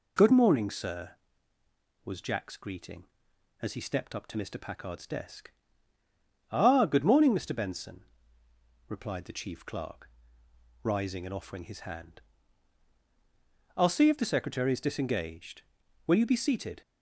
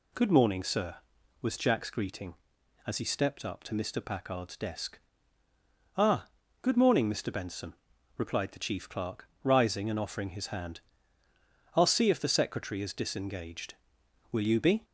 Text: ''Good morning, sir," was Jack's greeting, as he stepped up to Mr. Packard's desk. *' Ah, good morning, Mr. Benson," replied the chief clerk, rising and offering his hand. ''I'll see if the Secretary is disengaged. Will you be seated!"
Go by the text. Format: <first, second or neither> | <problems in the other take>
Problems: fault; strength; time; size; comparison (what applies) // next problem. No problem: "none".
first | stops before "seated"; at 14.8 s